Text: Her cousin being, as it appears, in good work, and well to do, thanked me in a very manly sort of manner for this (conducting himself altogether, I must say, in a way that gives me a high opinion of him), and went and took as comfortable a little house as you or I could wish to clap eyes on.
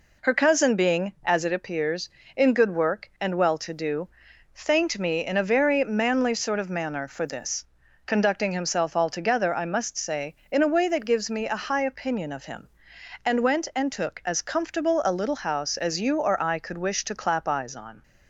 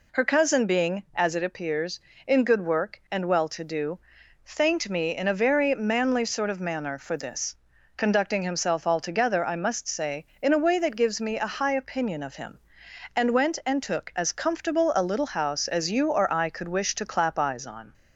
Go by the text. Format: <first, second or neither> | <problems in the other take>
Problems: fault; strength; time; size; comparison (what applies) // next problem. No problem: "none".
second | gets quieter; slight; throughout; 3.5 dB